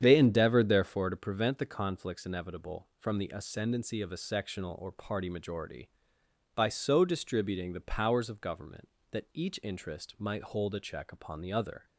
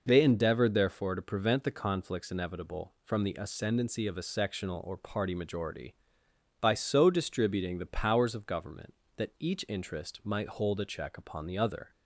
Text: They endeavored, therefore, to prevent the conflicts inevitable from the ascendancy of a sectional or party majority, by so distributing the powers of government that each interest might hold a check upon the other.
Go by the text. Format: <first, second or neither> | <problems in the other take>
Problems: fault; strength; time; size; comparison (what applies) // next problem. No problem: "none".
second | starts louder than the rest; strong; until 1.3 s; 8.5 dB